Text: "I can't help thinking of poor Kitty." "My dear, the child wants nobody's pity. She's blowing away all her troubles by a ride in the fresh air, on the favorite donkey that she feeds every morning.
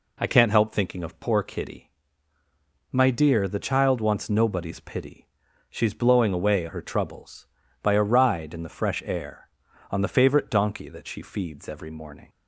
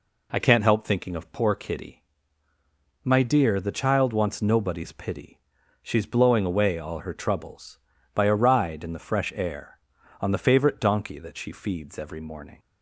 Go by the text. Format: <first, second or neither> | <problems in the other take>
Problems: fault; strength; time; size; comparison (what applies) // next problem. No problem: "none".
second | skips "all"; at 6.6 s